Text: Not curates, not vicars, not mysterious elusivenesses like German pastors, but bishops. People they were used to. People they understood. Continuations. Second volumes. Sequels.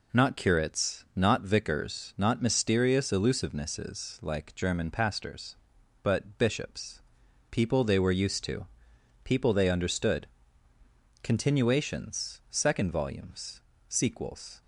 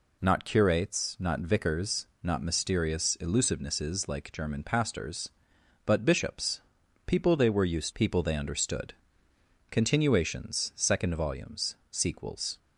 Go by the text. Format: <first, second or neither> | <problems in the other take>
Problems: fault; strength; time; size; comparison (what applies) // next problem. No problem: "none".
first | skips "to"; at 7.9 s